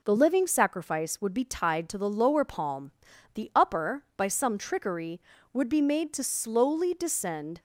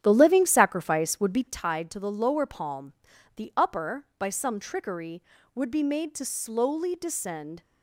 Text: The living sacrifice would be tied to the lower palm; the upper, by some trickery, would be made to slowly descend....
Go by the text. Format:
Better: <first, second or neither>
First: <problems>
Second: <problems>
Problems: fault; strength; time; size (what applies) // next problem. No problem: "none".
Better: first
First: none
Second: starts louder than the rest; strong; until 1.6 s; 9.5 dB